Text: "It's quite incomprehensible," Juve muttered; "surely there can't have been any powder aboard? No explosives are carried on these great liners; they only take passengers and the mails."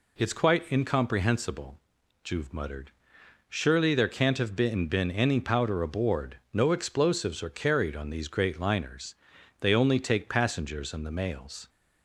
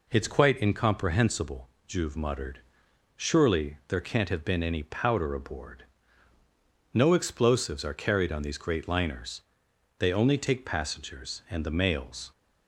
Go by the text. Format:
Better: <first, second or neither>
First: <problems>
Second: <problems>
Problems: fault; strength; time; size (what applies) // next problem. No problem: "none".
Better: second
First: says "been" twice; at 4.8 s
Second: none